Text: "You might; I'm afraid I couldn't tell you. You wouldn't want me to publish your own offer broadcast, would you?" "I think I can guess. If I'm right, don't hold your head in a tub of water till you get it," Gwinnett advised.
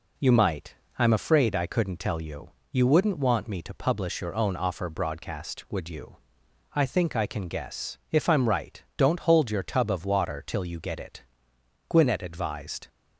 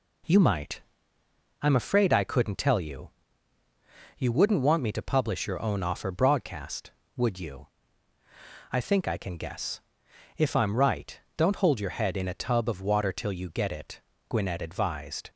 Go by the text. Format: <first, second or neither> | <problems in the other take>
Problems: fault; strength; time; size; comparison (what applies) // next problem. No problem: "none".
second | skips "head in a"; at 9.6 s